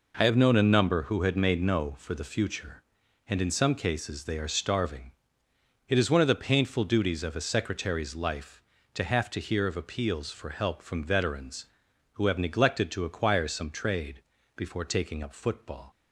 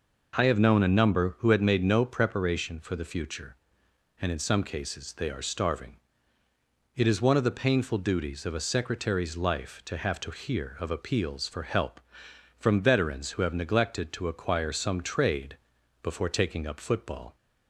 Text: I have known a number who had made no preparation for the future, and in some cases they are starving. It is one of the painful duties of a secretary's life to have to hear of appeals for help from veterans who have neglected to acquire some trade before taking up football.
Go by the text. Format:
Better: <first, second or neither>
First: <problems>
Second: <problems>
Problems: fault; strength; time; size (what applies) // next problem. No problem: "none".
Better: second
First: skips "preparation"; at 1.9 s // pauses between "trade" and "before"; slight; at 14.2 s; 0.34 s long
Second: pauses between "trade" and "before"; at 15.5 s; 0.44 s long